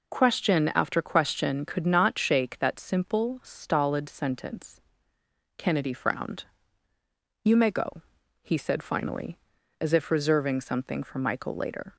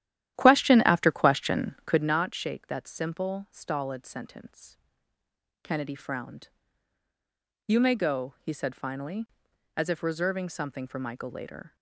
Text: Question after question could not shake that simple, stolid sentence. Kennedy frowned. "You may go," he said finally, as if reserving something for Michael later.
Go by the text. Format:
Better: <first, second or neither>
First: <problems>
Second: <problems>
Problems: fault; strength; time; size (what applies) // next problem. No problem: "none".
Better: first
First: none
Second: starts louder than the rest; strong; until 2.2 s; 12 dB